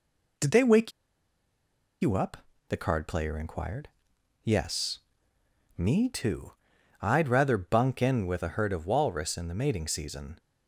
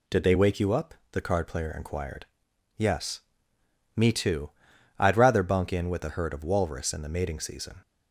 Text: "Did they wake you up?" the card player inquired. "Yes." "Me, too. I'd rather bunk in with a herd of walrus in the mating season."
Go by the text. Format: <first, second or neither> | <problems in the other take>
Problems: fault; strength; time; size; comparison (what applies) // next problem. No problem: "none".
second | pauses between "wake" and "you"; at 0.9 s; 1.1 s long